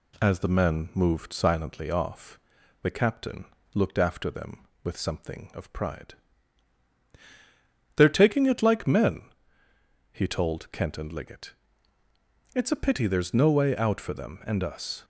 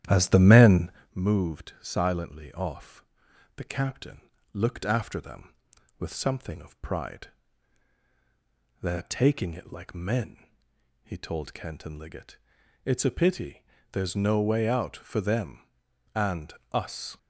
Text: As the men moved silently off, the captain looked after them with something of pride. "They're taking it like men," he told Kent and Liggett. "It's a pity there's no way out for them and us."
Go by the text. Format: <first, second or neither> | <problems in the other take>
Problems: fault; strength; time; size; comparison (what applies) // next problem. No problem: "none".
first | starts louder than the rest; strong; until 1.2 s; 11.5 dB // pauses between "men" and "moved"; slight; at 0.9 s; 0.24 s long // pauses between "captain" and "looked"; slight; at 4.2 s; 0.32 s long; slight in the first // pauses between "pity" and "there's"; slight; at 13.6 s; 0.28 s long // pauses between "and" and "us"; slight; at 16.5 s; 0.18 s long